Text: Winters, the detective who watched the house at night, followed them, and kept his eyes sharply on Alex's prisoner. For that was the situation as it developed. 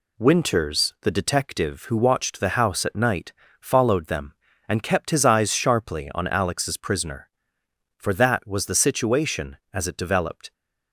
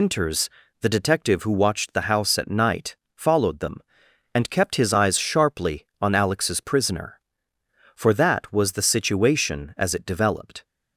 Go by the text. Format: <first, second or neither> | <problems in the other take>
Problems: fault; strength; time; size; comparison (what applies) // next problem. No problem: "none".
first | loses the start of "Winters"; at 0.0 s; 150 ms